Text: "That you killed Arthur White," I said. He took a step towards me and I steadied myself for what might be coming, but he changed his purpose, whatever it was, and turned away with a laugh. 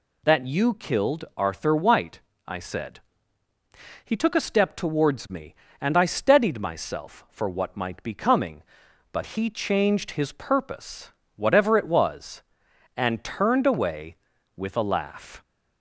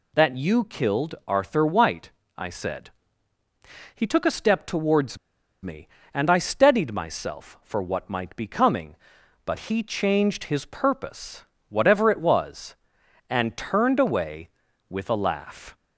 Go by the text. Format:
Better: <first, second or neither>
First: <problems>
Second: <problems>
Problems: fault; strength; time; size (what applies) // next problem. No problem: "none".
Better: first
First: none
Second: pauses between "towards" and "me"; noticeable; at 5.1 s; 0.46 s long